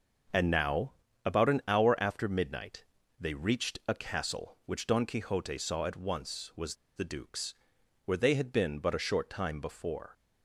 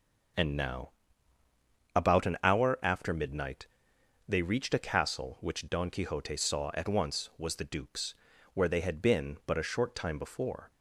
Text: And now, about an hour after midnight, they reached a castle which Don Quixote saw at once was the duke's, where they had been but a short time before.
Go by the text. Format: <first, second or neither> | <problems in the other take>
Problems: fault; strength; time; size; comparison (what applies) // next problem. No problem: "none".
second | starts louder than the rest; noticeable; until 1.7 s; 6 dB // pauses between "was" and "the"; slight; at 6.7 s; 0.20 s long